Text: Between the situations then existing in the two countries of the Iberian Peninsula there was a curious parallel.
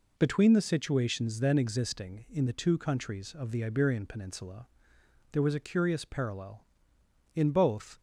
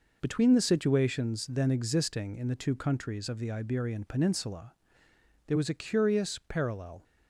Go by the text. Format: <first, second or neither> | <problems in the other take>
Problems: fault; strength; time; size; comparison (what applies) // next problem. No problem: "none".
second | pauses between "Peninsula" and "there"; noticeable; at 4.6 s; 0.64 s long; noticeable in the second // goes on to say "In both"; noticeable; from 7.3 s on; 0.64 s long